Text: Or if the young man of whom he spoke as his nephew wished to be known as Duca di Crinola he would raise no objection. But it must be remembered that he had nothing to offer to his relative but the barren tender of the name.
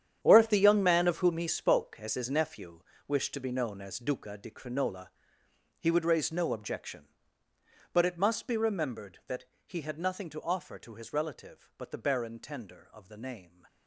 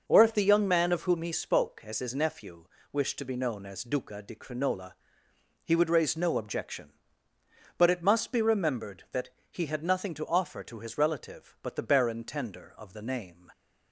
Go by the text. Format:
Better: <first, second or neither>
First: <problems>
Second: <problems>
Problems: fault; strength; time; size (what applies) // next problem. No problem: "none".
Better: second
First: gets quieter; strong; throughout; 14 dB // pauses between "nephew" and "wished"; slight; at 2.8 s; 0.26 s long // pauses between "Crinola" and "he"; noticeable; at 5.0 s; 0.70 s long // pauses between "that" and "he"; slight; at 9.4 s; 0.20 s long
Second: pauses between "nephew" and "wished"; slight; at 2.6 s; 0.26 s long // pauses between "Crinola" and "he"; noticeable; at 4.9 s; 0.70 s long // pauses between "that" and "he"; slight; at 9.3 s; 0.20 s long